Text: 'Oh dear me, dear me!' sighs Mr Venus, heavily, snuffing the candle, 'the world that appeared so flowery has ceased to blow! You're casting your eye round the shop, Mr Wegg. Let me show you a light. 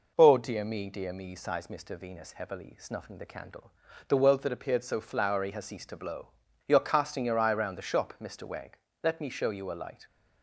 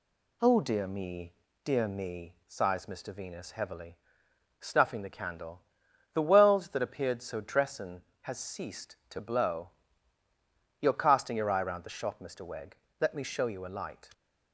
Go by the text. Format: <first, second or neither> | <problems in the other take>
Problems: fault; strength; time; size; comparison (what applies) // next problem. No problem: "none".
first | says "dressin" for "flowery"; at 7.3 s